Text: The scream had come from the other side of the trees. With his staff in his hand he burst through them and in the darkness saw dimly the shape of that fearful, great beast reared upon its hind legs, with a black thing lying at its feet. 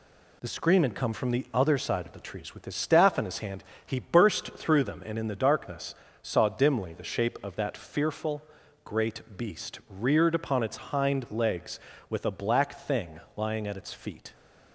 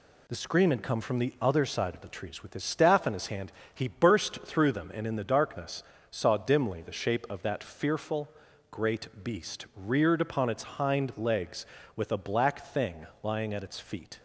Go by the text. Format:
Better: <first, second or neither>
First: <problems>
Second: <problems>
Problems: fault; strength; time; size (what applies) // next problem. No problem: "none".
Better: neither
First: pauses between "hand" and "he"; slight; at 3.6 s; 0.22 s long // pauses between "darkness" and "saw"; slight; at 5.9 s; 0.28 s long // pauses between "thing" and "lying"; slight; at 13.2 s; 0.16 s long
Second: pauses between "hand" and "he"; slight; at 3.5 s; 0.22 s long // pauses between "darkness" and "saw"; slight; at 5.8 s; 0.28 s long // pauses between "thing" and "lying"; slight; at 13.0 s; 0.16 s long